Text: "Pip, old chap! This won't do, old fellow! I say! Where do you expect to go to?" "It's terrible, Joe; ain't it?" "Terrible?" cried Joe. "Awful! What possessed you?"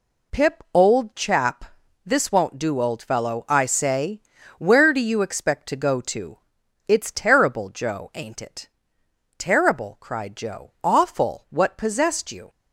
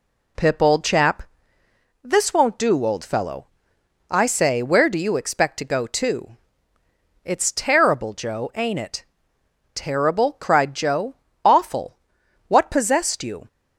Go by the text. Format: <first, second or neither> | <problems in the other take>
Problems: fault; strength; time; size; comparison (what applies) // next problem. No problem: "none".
neither | none